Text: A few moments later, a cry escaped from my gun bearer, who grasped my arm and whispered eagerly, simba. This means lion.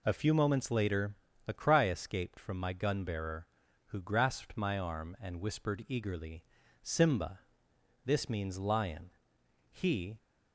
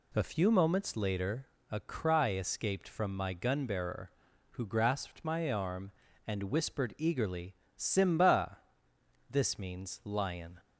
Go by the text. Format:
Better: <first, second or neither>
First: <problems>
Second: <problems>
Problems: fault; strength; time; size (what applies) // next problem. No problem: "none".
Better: second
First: goes on to say "He"; slight; from 9.7 s on; 0.46 s long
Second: none